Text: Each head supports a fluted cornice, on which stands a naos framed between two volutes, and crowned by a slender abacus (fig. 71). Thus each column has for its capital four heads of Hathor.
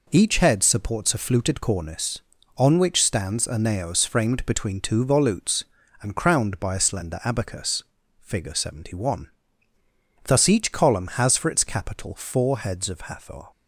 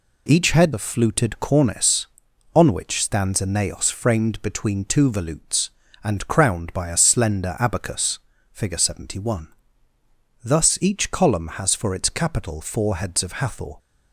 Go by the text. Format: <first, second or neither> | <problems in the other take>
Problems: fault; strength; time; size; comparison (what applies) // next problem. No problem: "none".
first | skips "supports"; at 0.7 s